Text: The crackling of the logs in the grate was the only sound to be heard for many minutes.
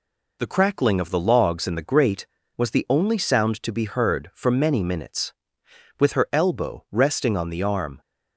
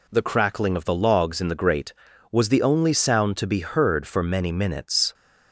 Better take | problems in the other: second | goes on to say "With her elbow resting on the arm"; strong; from 6.0 s on; 2.0 s long

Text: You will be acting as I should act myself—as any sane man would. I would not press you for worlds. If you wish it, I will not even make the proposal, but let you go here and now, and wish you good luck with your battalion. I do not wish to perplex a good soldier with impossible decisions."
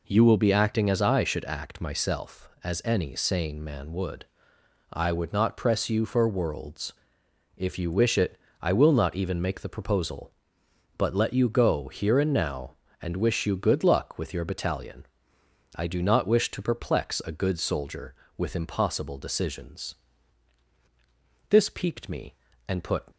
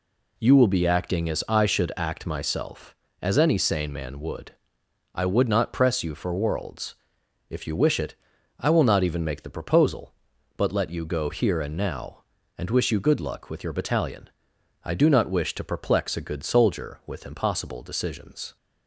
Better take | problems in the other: second | goes on to say "This piqued me and put"; from 21.4 s on; 1.5 s long

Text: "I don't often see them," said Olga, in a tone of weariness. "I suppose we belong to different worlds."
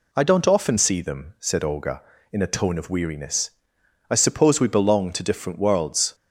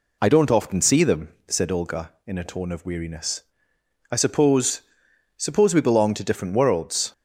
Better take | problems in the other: first | says "suppose" twice; at 5.3 s

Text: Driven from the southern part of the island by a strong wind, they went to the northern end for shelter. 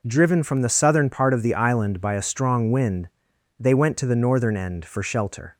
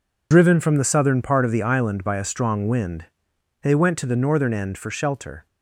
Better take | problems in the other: first | loses the start of "Driven"; at 0.3 s; 85 ms

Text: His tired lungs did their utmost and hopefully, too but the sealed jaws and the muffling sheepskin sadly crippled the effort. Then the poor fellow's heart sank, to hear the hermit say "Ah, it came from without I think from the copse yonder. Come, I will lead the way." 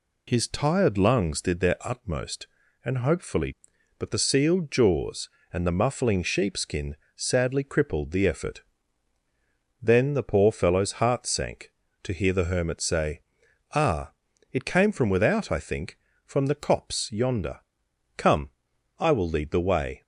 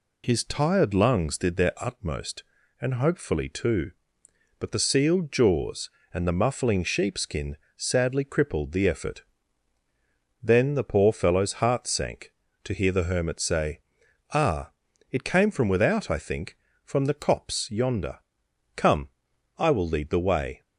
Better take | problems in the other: second | skips "too"; at 3.7 s // pauses between "sheepskin" and "sadly"; slight; at 6.9 s; 0.20 s long; slight in the second // pauses between "say" and "Ah"; noticeable; at 13.2 s; 0.52 s long; noticeable in the second

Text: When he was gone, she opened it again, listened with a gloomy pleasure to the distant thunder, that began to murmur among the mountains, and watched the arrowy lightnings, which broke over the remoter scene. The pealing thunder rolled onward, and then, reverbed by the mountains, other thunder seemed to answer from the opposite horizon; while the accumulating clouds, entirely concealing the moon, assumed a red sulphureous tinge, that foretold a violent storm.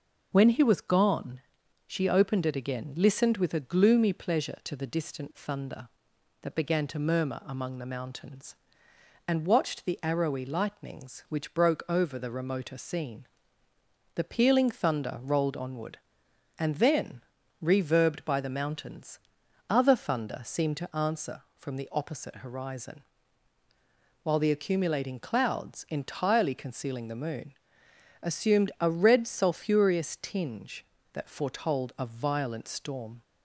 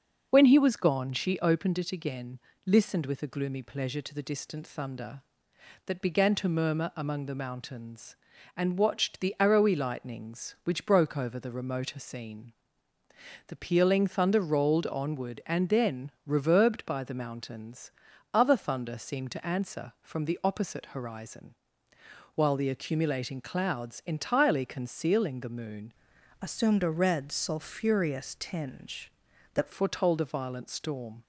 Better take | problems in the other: first | changes voice from "assumed" to "that"; from 26.4 to 29.7 s; 3.3 s long

